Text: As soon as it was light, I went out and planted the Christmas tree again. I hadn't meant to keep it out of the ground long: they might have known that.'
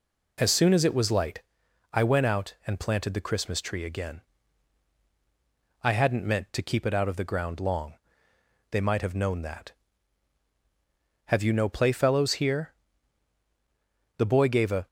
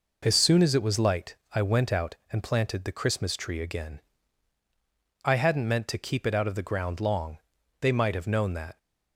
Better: second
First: goes on to say "Have you no playfellows here The boy gave a"; strong; from 11.2 s on; 3.6 s long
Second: none

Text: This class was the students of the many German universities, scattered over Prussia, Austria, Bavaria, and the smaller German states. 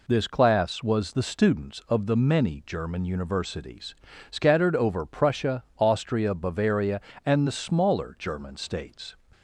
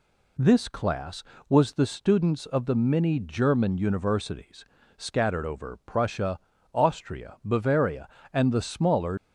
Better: first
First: none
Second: stops before "German states"; at 9.1 s

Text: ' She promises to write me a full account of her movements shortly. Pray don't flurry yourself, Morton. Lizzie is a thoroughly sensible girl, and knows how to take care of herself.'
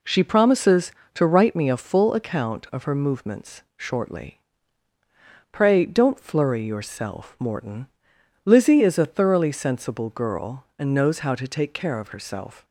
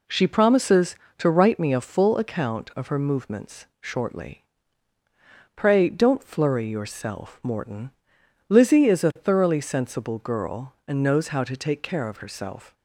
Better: neither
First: none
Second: none

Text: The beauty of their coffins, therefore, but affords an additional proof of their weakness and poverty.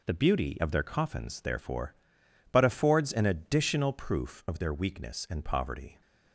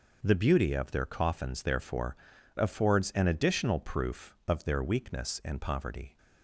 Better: first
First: none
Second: skips "but"; at 2.3 s

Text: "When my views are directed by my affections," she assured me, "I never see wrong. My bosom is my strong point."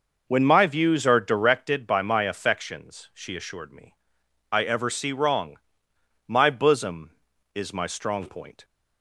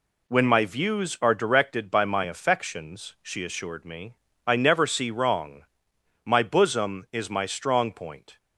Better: second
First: says "ever" for "never"; at 4.6 s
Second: none

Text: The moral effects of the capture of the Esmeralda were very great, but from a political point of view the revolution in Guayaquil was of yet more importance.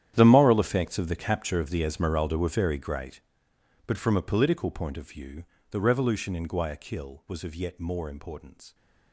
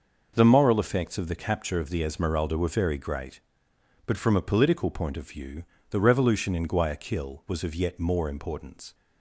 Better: second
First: gets quieter; strong; throughout; 17 dB // pauses between "view" and "the"; slight; at 5.4 s; 0.28 s long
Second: pauses between "view" and "the"; slight; at 5.6 s; 0.28 s long

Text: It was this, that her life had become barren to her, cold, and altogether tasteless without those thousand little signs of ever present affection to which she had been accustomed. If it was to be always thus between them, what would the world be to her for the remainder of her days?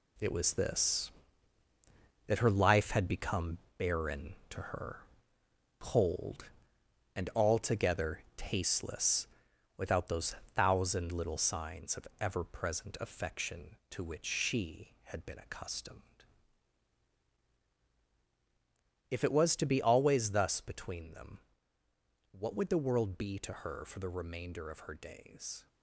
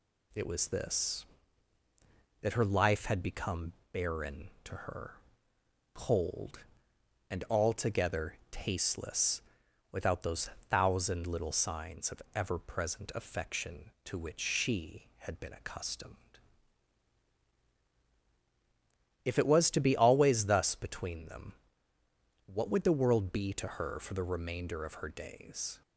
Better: second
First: gets quieter; strong; throughout; 8 dB // pauses between "become" and "barren"; slight; at 3.5 s; 0.18 s long // pauses between "tasteless" and "without"; noticeable; at 9.2 s; 0.50 s long // pauses between "those" and "thousand"; slight; at 10.3 s; 0.20 s long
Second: pauses between "become" and "barren"; slight; at 3.7 s; 0.18 s long // pauses between "tasteless" and "without"; noticeable; at 9.4 s; 0.50 s long // pauses between "those" and "thousand"; slight; at 10.4 s; 0.20 s long

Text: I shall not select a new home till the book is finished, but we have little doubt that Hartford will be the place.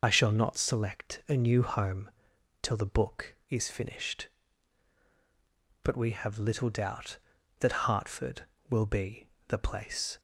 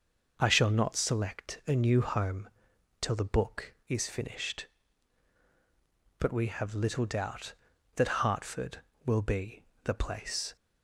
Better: second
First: loses the start of "I"; at 0.0 s; 40 ms // pauses between "home" and "till"; noticeable; at 2.1 s; 0.50 s long // pauses between "be" and "the"; slight; at 9.2 s; 0.20 s long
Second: pauses between "home" and "till"; noticeable; at 2.4 s; 0.50 s long // pauses between "be" and "the"; slight; at 9.6 s; 0.20 s long

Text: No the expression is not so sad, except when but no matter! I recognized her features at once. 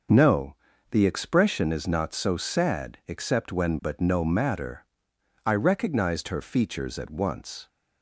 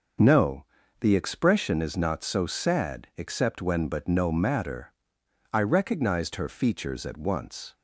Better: neither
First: pauses between "No" and "the"; slight; at 0.5 s; 0.34 s long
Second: pauses between "No" and "the"; slight; at 0.6 s; 0.34 s long

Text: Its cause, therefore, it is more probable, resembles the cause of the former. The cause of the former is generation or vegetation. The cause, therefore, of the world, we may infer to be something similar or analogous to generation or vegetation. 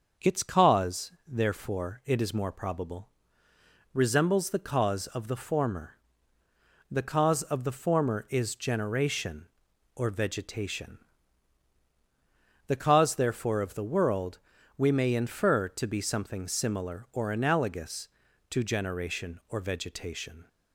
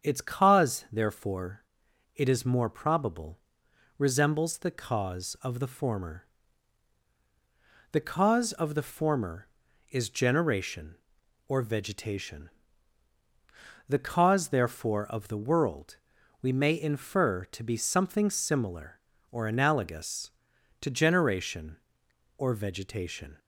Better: neither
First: starts louder than the rest; until 1.3 s; 6.5 dB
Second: starts louder than the rest; strong; until 1.1 s; 7.5 dB

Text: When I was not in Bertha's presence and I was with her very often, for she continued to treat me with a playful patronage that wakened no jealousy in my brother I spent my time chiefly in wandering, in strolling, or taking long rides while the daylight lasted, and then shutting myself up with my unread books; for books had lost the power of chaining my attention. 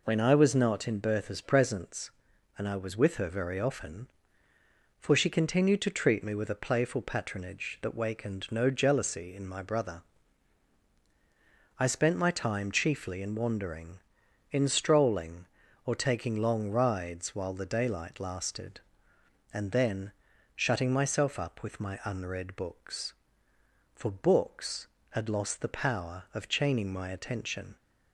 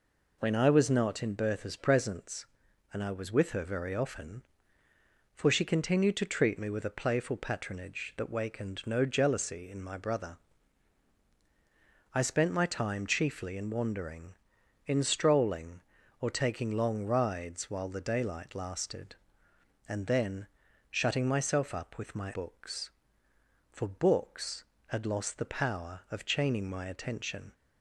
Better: first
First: pauses between "brother" and "I"; strong; at 10.0 s; 1.7 s long // pauses between "then" and "shutting"; at 20.1 s; 0.42 s long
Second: pauses between "brother" and "I"; strong; at 10.3 s; 1.7 s long // pauses between "then" and "shutting"; at 20.4 s; 0.42 s long // skips "unread"; at 22.3 s

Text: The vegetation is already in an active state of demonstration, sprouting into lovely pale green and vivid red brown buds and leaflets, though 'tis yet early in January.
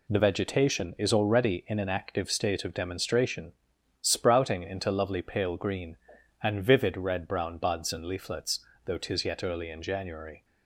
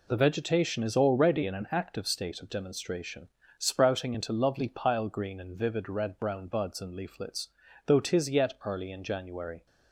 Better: first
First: none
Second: says "pile" for "pale"; at 4.6 s

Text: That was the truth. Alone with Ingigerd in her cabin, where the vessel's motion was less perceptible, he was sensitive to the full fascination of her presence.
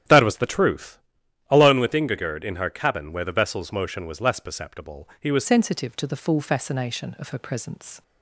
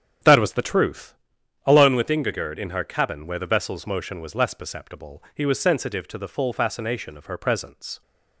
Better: second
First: starts louder than the rest; strong; until 1.6 s; 10.5 dB // changes voice at "sensitive"; from 5.4 s on; 2.6 s long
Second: starts louder than the rest; strong; until 1.7 s; 9 dB

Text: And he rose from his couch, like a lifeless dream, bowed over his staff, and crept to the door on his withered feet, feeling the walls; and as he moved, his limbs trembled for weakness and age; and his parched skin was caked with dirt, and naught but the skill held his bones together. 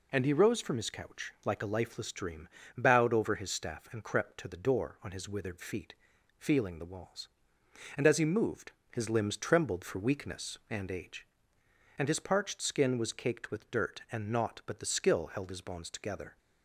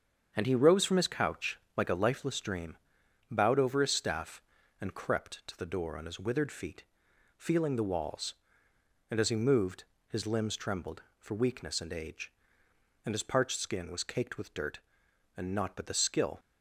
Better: first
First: none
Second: starts louder than the rest; strong; until 1.3 s; 7 dB // stops before "held his bones together"; at 16.3 s

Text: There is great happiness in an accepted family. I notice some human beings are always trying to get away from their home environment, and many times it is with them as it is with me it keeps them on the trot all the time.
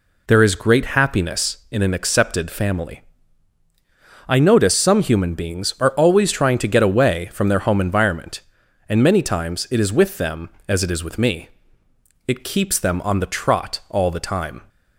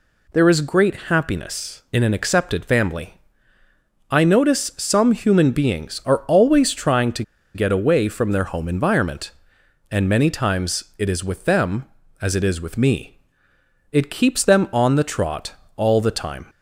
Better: first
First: pauses between "me" and "it"; noticeable; at 11.4 s; 0.78 s long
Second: pauses between "to" and "get"; slight; at 7.2 s; 0.32 s long // pauses between "me" and "it"; noticeable; at 13.1 s; 0.76 s long // pauses between "trot" and "all"; slight; at 15.5 s; 0.22 s long

